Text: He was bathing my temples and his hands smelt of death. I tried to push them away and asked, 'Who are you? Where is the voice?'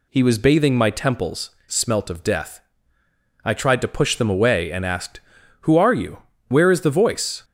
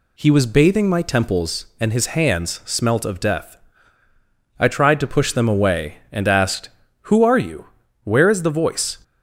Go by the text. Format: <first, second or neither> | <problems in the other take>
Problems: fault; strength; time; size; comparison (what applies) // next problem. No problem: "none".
second | skips "and his hands"; at 1.6 s